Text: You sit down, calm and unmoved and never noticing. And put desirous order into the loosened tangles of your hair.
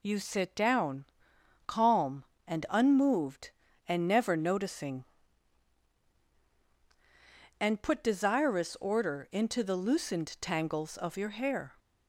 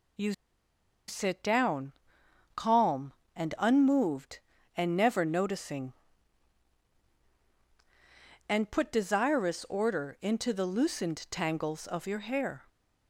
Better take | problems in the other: first | pauses between "You" and "sit"; noticeable; at 0.3 s; 0.76 s long

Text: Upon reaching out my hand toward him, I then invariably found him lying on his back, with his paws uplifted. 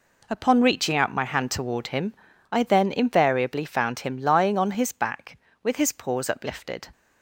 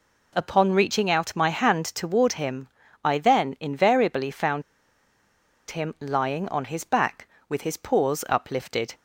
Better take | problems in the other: first | pauses between "found" and "him"; at 4.6 s; 1.0 s long

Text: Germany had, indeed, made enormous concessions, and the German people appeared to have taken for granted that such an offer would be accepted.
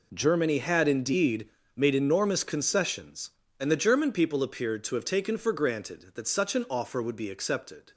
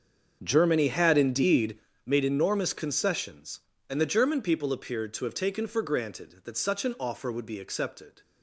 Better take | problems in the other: first | starts louder than the rest; until 2.0 s; 6.5 dB

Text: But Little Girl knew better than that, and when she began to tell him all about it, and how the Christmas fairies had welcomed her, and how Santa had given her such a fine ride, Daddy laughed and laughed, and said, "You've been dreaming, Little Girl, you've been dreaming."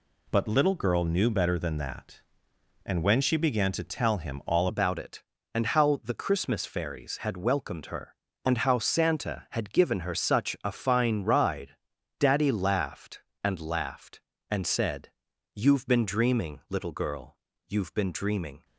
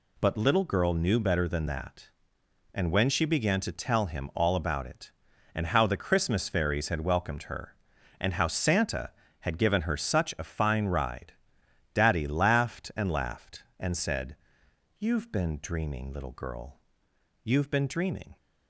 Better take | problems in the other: second | changes voice at "about"; from 4.6 s on; 14.0 s long

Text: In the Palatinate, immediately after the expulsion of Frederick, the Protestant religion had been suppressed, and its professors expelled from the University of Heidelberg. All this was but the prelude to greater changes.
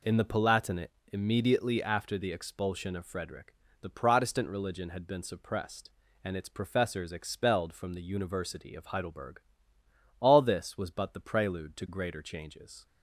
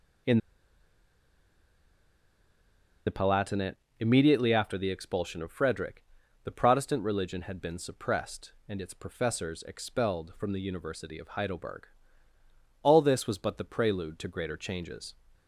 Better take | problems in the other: first | pauses between "In" and "the"; strong; at 0.3 s; 2.6 s long

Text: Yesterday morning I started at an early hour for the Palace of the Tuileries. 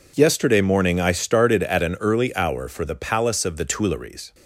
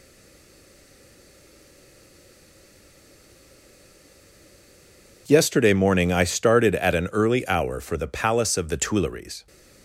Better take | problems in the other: first | stays silent before the first word; strong; until 5.2 s; 5.2 s long

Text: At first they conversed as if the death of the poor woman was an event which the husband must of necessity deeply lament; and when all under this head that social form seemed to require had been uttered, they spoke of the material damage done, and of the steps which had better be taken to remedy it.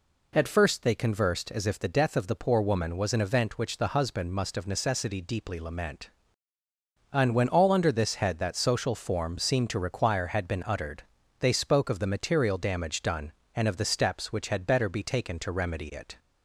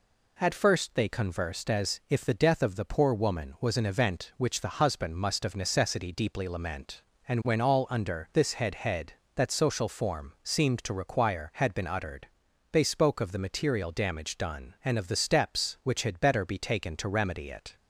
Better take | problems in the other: first | says "head" twice; at 8.7 s

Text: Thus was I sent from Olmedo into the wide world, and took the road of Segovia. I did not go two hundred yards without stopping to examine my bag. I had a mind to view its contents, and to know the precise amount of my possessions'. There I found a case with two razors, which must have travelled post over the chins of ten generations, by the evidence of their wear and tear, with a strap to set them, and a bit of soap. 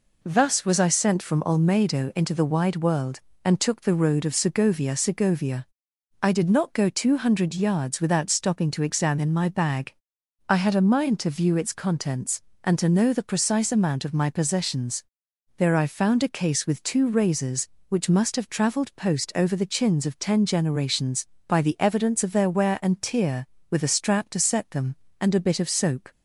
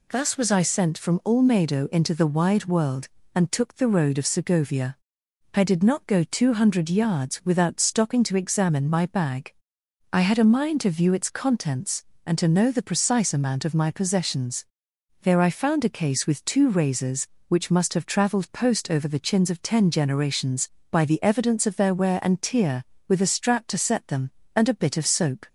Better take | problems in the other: second | says "Segovia" twice; at 4.9 s

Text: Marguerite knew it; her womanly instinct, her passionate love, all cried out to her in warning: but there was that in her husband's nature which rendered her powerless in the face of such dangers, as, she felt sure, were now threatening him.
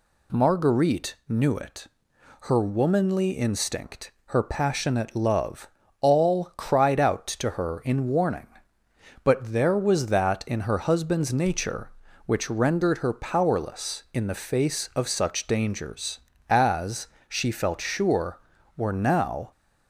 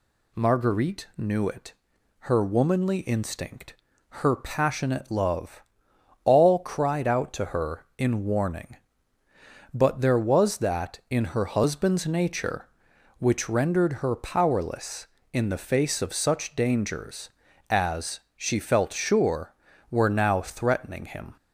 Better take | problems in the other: second | stops before "threatening him"; at 19.5 s

